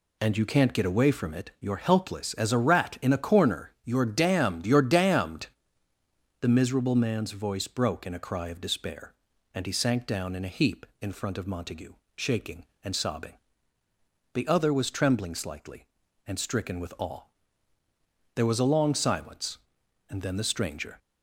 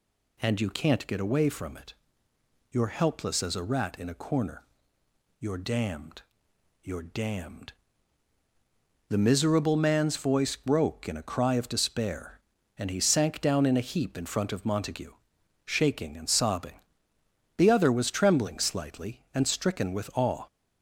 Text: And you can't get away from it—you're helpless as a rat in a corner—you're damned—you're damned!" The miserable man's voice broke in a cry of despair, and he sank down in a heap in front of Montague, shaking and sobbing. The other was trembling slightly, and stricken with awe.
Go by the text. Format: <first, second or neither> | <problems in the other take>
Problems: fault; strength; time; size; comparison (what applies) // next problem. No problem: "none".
second | goes on to say "There was a long silence and then the stranger"; strong; from 18.3 s on; 2.6 s long